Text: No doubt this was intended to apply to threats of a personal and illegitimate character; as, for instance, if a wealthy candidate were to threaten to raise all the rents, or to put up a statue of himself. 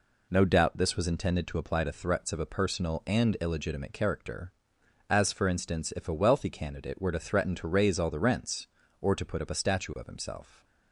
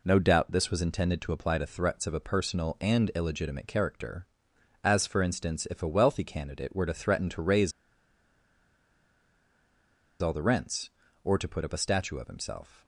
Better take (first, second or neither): first